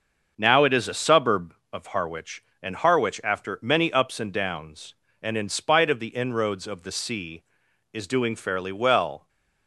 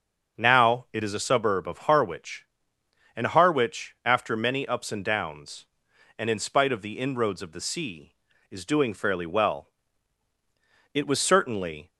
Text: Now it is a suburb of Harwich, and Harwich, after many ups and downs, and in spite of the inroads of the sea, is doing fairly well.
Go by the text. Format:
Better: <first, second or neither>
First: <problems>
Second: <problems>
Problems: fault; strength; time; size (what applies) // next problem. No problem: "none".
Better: first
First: starts louder than the rest; until 1.3 s; 6.5 dB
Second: starts louder than the rest; until 1.4 s; 6.5 dB // goes on to say "It was certainly"; noticeable; from 10.9 s on; 0.96 s long